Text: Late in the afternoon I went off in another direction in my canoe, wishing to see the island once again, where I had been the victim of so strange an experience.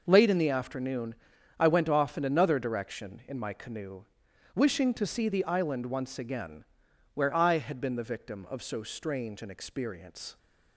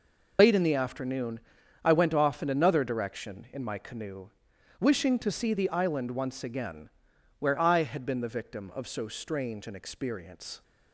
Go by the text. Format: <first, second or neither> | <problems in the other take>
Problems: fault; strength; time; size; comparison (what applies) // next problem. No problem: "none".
first | loses the start of "Late"; at 0.3 s; 70 ms // pauses between "afternoon" and "I"; noticeable; at 1.3 s; 0.46 s long; noticeable in the first